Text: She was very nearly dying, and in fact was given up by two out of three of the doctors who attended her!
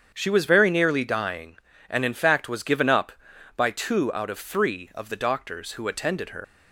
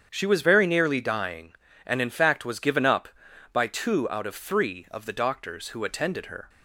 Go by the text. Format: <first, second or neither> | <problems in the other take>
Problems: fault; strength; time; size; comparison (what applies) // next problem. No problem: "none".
second | starts louder than the rest; strong; until 1.1 s; 7.5 dB; strong in the second // leaves "her" unfinished; at 6.4 s; 80 ms